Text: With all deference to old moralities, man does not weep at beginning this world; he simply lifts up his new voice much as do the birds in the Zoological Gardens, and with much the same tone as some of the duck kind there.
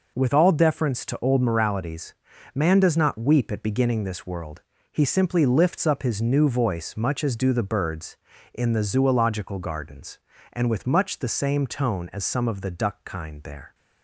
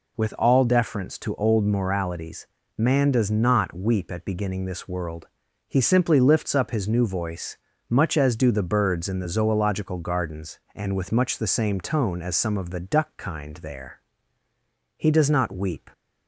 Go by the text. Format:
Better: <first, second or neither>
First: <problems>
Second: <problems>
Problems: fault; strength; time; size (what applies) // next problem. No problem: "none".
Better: first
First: none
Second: pauses between "voice" and "much"; slight; at 7.5 s; 0.32 s long // goes on to say "He does not weep"; noticeable; from 14.9 s on; 0.92 s long